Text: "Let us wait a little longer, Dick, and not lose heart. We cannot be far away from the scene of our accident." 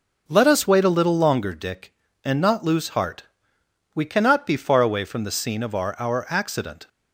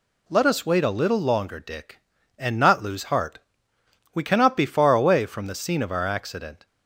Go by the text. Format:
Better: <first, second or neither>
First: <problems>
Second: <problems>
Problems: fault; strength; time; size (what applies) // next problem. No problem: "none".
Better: second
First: says "our" twice; at 5.9 s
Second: none